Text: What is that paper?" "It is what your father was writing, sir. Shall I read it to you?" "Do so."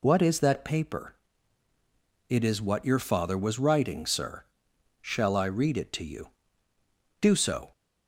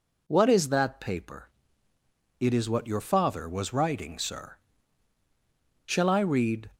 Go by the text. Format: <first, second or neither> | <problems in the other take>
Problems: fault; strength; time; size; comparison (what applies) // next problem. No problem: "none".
first | stops before "it to you Do so"; at 6.7 s